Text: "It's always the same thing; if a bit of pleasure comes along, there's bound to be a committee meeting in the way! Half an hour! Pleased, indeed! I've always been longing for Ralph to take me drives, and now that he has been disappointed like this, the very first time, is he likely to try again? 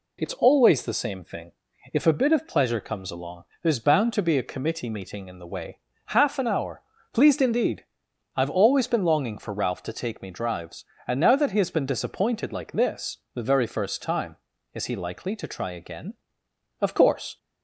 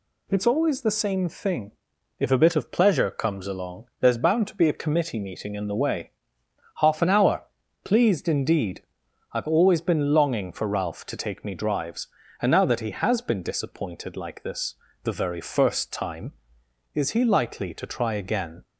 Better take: second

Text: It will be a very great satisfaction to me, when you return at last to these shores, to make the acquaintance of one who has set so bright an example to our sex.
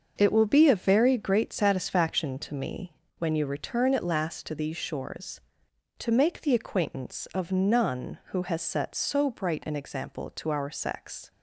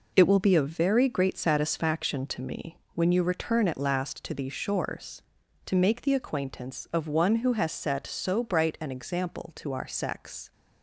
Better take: second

